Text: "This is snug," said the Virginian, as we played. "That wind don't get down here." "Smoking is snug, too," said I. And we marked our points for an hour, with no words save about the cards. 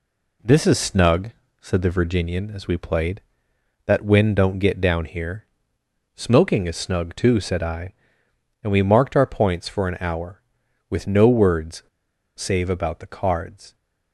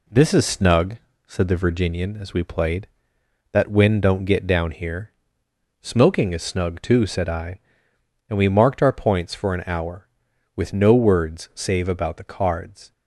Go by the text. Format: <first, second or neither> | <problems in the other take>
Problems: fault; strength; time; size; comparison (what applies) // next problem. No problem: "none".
second | pauses between "words" and "save"; noticeable; at 11.8 s; 0.53 s long